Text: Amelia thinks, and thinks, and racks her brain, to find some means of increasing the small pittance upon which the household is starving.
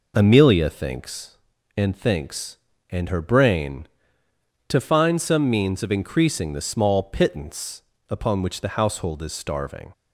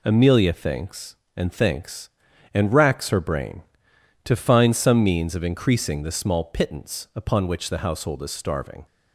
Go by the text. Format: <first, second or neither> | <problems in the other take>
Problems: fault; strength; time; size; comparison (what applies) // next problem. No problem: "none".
second | skips "racks"; at 3.0 s // pauses between "pittance" and "upon"; slight; at 7.8 s; 0.26 s long